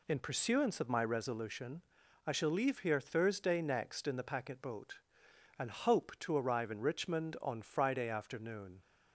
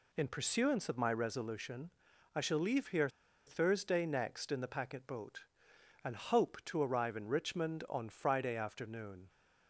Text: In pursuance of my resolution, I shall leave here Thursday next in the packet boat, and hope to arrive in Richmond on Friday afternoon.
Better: first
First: none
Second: pauses between "here" and "Thursday"; at 3.0 s; 0.38 s long

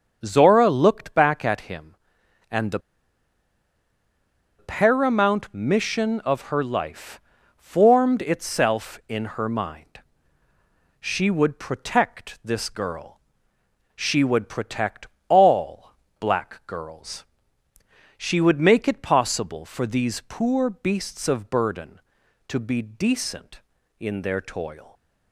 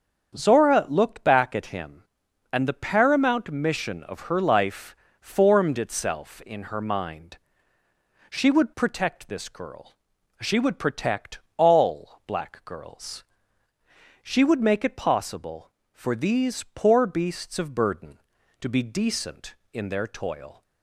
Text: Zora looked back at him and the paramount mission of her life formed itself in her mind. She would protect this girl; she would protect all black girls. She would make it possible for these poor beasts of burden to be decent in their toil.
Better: second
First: starts louder than the rest; until 1.2 s; 6.5 dB // pauses between "the" and "paramount"; strong; at 2.7 s; 1.7 s long // pauses between "life" and "formed"; at 7.1 s; 0.38 s long // pauses between "protect" and "all"; slight; at 15.0 s; 0.20 s long // pauses between "all" and "black"; slight; at 15.9 s; 0.26 s long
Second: starts louder than the rest; strong; until 1.3 s; 7.5 dB // pauses between "life" and "formed"; slight; at 4.9 s; 0.24 s long // pauses between "protect" and "all"; slight; at 11.3 s; 0.18 s long

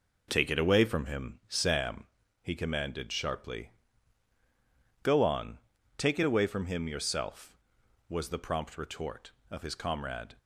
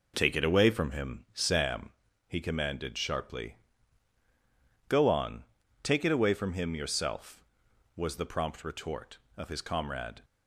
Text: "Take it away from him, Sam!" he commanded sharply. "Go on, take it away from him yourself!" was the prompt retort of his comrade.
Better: neither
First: none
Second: none

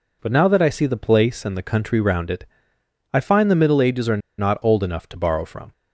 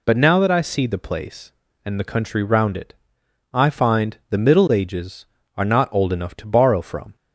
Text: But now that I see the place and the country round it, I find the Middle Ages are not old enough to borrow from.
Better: second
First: pauses between "are" and "not"; slight; at 4.1 s; 0.20 s long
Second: none

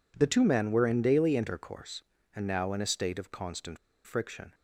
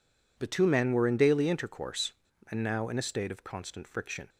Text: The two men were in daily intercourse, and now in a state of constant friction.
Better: second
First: pauses between "constant" and "friction"; slight; at 3.7 s; 0.27 s long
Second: none

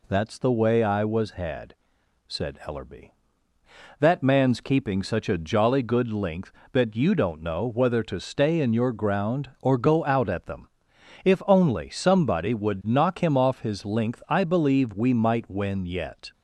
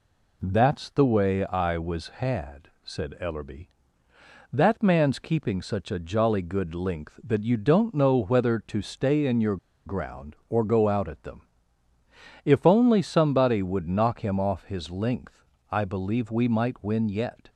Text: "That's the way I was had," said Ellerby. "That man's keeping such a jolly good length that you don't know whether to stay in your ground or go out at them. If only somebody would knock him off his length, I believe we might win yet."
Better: first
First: none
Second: pauses between "your" and "ground"; slight; at 9.5 s; 0.29 s long

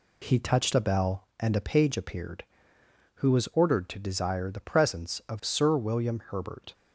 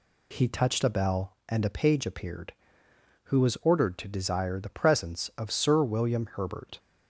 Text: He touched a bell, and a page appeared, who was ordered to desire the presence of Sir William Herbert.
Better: second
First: gets quieter; slight; throughout; 2.5 dB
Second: none

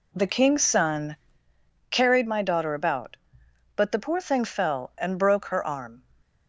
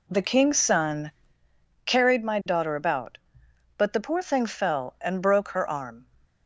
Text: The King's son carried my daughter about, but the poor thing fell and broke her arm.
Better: neither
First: pauses between "son" and "carried"; noticeable; at 1.1 s; 0.74 s long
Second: pauses between "son" and "carried"; noticeable; at 1.1 s; 0.74 s long

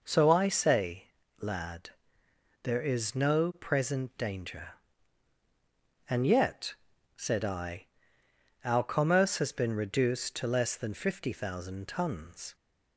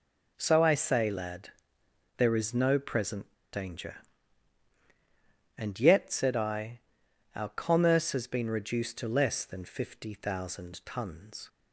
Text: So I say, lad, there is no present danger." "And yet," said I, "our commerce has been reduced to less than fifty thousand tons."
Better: first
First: none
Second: pauses between "present" and "danger"; slight; at 3.3 s; 0.19 s long

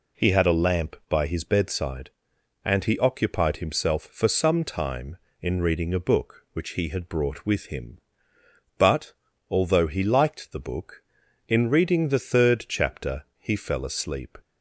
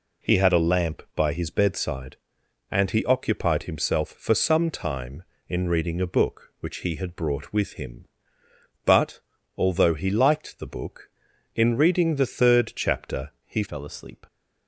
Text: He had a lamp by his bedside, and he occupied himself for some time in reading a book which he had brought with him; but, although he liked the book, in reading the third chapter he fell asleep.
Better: first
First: none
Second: changes voice at "fell"; from 13.6 s on; 0.6 s long

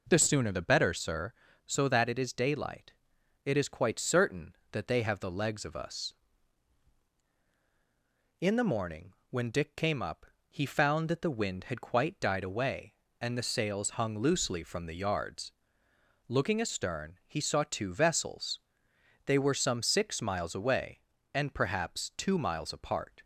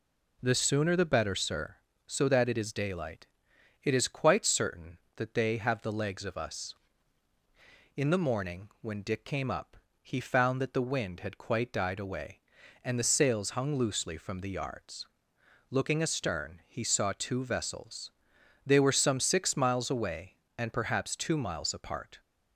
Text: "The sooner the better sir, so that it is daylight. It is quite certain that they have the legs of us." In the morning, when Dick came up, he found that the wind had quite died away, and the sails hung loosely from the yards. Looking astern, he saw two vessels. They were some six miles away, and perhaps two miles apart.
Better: neither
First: none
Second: none

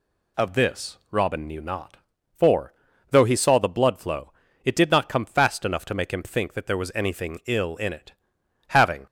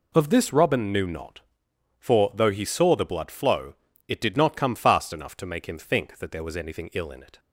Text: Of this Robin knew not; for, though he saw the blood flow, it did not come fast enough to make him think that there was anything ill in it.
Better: second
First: pauses between "this" and "Robin"; slight; at 0.9 s; 0.16 s long // goes on to say "Having"; slight; from 8.6 s on; 0.36 s long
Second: none

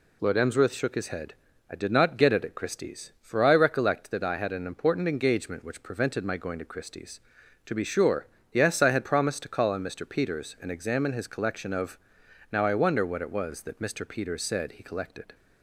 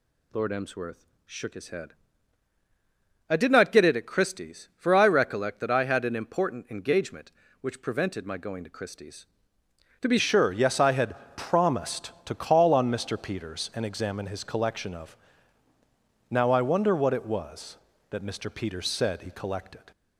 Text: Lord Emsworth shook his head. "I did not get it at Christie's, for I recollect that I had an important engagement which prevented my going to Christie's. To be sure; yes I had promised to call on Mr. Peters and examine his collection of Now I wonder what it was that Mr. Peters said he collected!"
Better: first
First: pauses between "of" and "Now"; noticeable; at 11.9 s; 0.54 s long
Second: pauses between "Emsworth" and "shook"; slight; at 1.0 s; 0.20 s long // changes voice at "sure"; from 10.1 s on; 9.8 s long // pauses between "had" and "promised"; slight; at 11.1 s; 0.20 s long // pauses between "of" and "Now"; at 15.1 s; 1.1 s long

